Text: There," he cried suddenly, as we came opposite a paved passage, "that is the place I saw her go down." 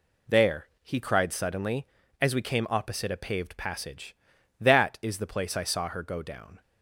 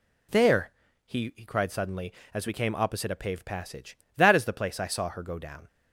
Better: first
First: none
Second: says "he" twice; at 1.3 s

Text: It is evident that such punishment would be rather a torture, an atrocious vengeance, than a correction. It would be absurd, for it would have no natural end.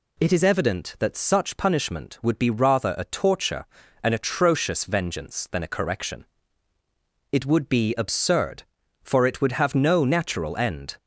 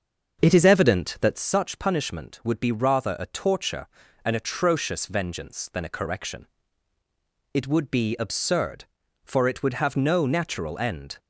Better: first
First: none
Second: starts louder than the rest; until 1.5 s; 6.5 dB

